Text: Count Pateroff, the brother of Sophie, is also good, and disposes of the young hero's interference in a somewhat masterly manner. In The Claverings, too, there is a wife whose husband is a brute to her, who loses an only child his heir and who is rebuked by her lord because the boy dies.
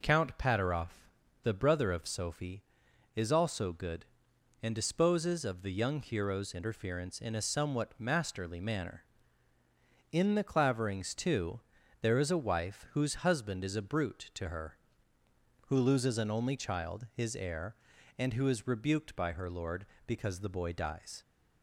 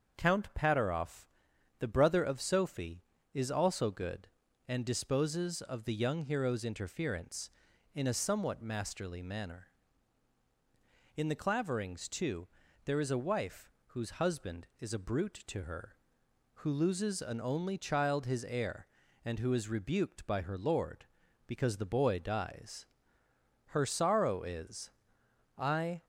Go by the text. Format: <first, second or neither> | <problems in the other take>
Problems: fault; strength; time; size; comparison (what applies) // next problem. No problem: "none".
first | starts louder than the rest; until 1.2 s; 7 dB // pauses between "wife" and "whose"; slight; at 13.7 s; 0.18 s long // goes on to say "Her sorrow is I"; strong; from 23.7 s on; 2.3 s long